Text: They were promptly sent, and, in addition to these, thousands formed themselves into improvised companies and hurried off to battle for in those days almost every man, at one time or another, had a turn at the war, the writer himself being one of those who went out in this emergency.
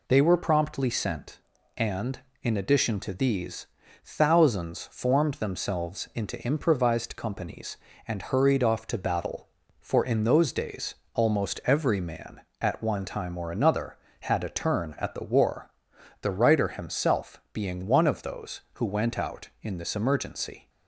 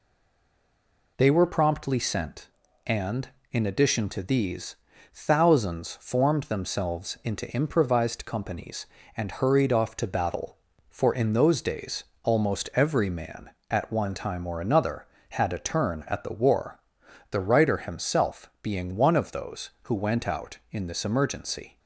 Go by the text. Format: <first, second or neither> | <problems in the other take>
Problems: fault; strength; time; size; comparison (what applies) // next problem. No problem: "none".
first | stays silent before the first word; noticeable; until 1.1 s; 1.1 s long // pauses between "days" and "almost"; slight; at 12.0 s; 0.20 s long; slight in the first